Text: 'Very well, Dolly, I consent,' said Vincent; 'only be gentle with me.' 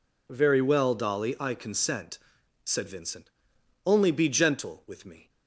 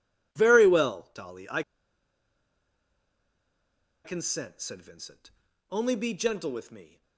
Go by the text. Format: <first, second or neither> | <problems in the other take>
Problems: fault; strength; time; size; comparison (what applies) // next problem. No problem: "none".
first | pauses between "I" and "consent"; strong; at 1.6 s; 2.4 s long